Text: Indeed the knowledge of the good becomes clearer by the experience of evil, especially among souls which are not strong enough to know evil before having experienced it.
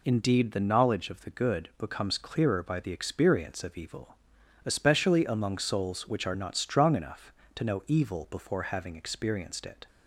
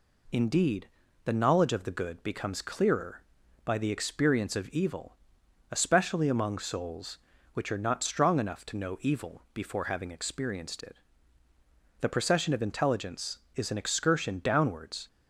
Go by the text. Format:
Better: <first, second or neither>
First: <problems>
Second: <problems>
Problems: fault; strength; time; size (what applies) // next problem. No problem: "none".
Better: first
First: none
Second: pauses between "Indeed" and "the"; slight; at 0.8 s; 0.36 s long // goes on to say "THE PROCESSION OF INTELLIGENCE IS AN EXCURSION DOWNWARDS"; strong; from 11.9 s on; 3.0 s long